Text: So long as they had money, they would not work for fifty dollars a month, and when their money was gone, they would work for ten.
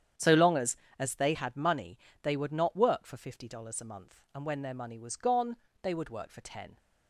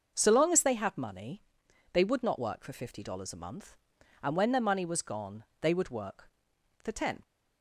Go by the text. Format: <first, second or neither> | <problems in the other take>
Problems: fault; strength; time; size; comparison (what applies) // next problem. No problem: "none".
second | starts louder than the rest; strong; until 1.4 s; 9 dB // says "as" twice; at 0.9 s